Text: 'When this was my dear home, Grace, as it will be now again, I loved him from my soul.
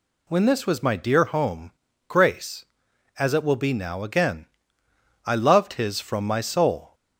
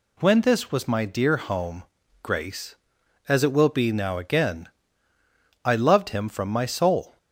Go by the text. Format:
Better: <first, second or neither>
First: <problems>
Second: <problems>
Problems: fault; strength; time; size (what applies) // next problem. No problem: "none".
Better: second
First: says "his" for "him"; at 5.7 s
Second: none